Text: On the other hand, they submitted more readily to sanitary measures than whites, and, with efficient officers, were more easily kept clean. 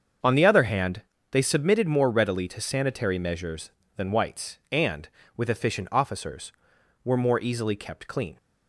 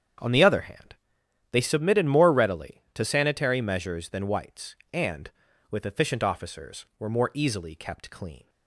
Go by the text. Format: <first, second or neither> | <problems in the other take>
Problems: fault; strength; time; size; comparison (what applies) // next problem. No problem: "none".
neither | starts louder than the rest; the same in both